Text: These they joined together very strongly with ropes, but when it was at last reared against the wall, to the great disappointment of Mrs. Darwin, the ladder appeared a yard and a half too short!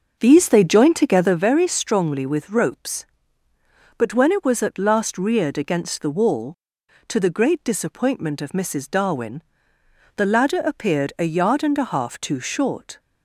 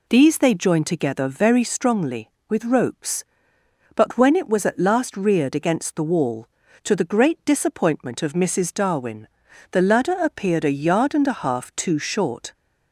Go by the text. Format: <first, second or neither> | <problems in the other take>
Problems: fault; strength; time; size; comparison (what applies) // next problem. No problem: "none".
second | starts louder than the rest; noticeable; until 1.4 s; 6 dB